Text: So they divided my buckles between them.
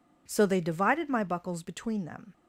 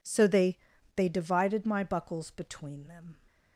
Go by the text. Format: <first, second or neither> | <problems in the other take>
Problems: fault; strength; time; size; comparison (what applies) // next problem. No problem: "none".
first | says "they" twice; at 0.9 s